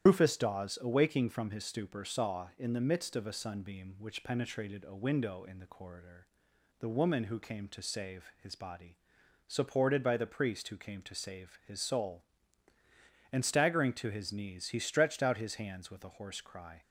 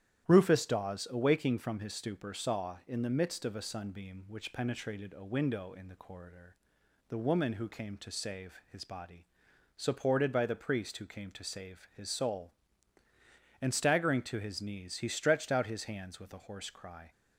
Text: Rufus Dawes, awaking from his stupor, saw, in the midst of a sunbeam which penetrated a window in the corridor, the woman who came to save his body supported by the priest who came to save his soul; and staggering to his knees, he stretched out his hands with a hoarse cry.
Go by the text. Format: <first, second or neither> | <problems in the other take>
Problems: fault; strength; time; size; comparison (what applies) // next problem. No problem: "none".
second | loses the start of "Rufus"; at 0.0 s; 85 ms // starts louder than the rest; strong; until 1.1 s; 10.5 dB; strong in the second // pauses between "body" and "supported"; noticeable; at 8.9 s; 0.50 s long; noticeable in the second